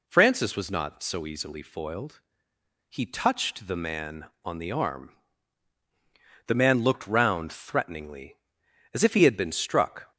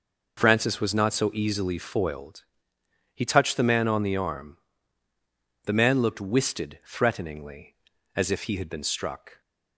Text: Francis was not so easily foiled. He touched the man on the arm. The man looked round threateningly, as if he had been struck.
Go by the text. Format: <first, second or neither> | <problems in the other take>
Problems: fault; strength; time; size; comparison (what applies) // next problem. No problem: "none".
first | says "wisted" for "round"; at 6.2 s